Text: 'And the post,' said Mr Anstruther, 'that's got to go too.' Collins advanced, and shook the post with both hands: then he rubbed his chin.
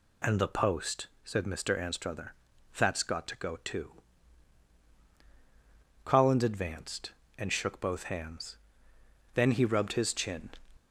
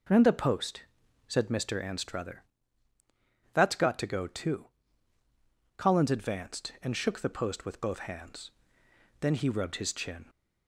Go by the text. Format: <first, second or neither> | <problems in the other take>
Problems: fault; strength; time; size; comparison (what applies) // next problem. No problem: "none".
second | skips "the post with"; at 7.8 s